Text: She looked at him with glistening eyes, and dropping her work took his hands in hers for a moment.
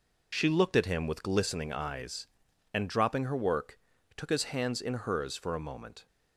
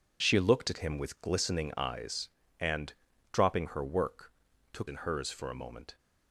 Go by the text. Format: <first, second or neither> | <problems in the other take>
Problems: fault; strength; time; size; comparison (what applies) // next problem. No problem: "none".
first | pauses between "and" and "dropping"; at 2.9 s; 0.38 s long // pauses between "work" and "took"; at 4.3 s; 0.40 s long; also in the first // skips "his hands"; at 4.8 s